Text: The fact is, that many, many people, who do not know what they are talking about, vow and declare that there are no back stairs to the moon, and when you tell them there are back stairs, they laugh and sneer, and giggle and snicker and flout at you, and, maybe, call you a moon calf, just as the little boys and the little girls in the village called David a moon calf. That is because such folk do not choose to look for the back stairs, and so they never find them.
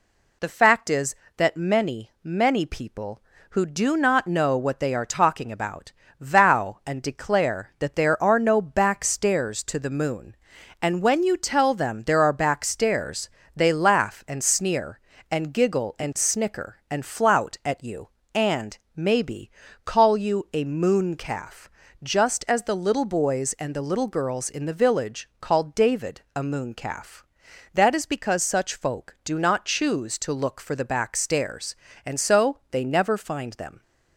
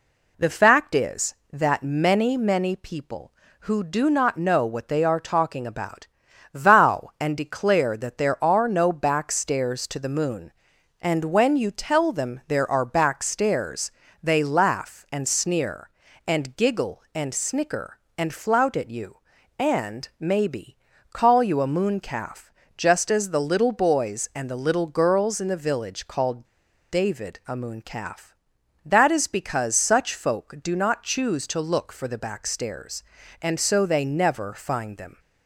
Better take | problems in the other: first | pauses between "called" and "David"; at 26.4 s; 0.45 s long

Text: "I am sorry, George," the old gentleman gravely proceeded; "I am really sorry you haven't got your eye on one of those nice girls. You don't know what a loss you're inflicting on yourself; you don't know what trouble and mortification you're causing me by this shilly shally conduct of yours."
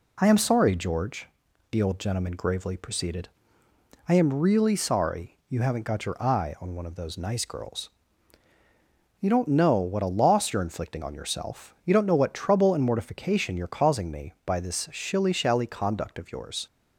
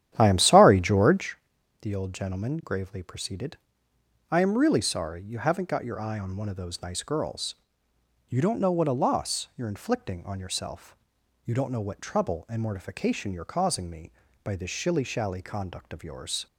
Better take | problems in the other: first | starts louder than the rest; strong; until 1.3 s; 11 dB

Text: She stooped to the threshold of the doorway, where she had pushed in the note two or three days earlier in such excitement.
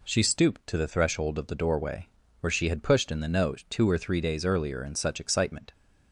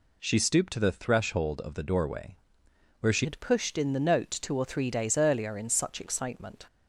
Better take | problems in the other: first | changes voice at "had"; from 3.2 s on; 3.4 s long

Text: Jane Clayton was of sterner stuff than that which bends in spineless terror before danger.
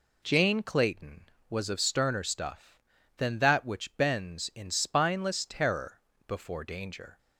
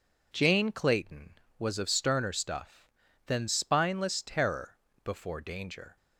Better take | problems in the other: first | skips "that which bends in"; at 3.4 s // pauses between "terror" and "before"; slight; at 4.7 s; 0.28 s long; slight in the first

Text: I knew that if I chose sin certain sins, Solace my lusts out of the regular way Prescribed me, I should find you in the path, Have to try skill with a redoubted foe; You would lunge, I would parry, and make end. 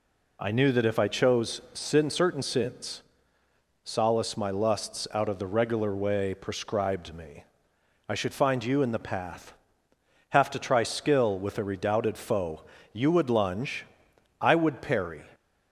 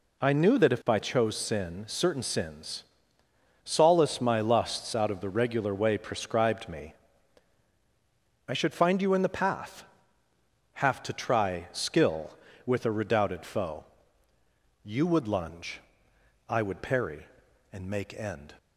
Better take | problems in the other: second | stops before "and make end"; at 15.3 s

